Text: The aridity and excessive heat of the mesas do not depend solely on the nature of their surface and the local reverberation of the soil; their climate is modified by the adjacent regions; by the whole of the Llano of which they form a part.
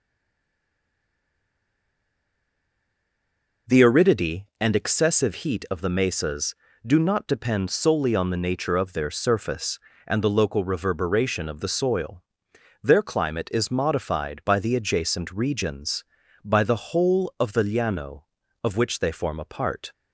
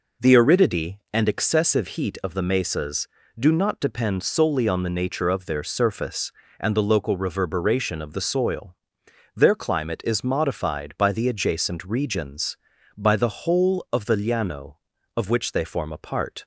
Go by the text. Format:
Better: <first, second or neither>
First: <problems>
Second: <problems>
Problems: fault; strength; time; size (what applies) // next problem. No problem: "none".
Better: second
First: stays silent before the first word; strong; until 3.6 s; 3.6 s long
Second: none